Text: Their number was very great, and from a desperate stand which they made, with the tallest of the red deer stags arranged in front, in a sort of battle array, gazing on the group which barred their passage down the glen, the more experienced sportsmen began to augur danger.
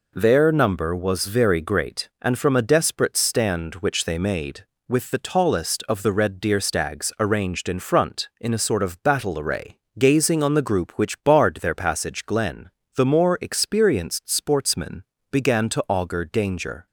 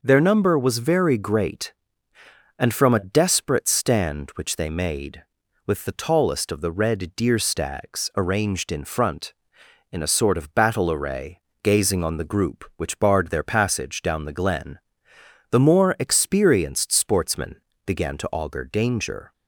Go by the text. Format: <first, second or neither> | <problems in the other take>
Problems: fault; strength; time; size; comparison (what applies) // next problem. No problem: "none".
second | skips "down the"; at 12.2 s // pauses between "sportsmen" and "began"; slight; at 15.0 s; 0.30 s long; slight in the second